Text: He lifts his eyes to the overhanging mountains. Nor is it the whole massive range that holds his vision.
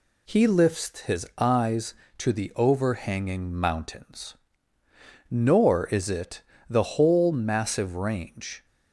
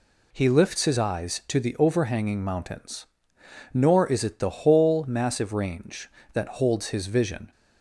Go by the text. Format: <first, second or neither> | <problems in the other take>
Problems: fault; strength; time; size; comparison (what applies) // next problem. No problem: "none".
second | pauses between "it" and "the"; slight; at 6.4 s; 0.26 s long // stops before "that holds his vision"; at 8.6 s